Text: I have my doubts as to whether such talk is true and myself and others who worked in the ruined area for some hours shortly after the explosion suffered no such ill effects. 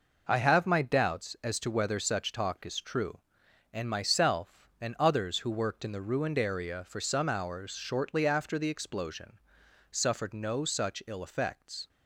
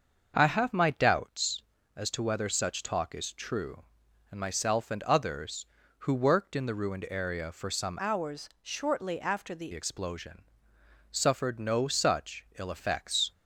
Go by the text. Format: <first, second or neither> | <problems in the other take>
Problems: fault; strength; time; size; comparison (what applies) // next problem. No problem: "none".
first | starts louder than the rest; until 1.3 s; 6.5 dB // changes voice from "hours" to "the"; from 7.9 to 9.7 s; 1.8 s long // pauses between "explosion" and "suffered"; noticeable; at 10.4 s; 0.68 s long; noticeable in the first